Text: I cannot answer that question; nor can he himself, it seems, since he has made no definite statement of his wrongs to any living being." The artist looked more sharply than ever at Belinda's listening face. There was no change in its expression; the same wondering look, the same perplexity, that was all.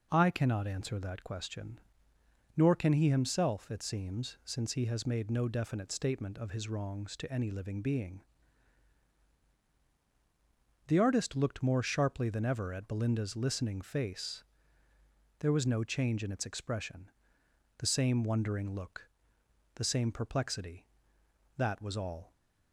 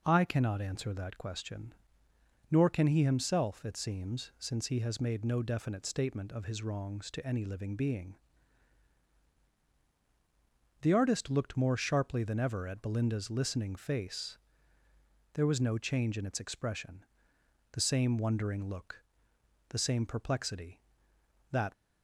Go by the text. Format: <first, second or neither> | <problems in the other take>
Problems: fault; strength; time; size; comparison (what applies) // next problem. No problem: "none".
first | stops before "was all"; at 21.7 s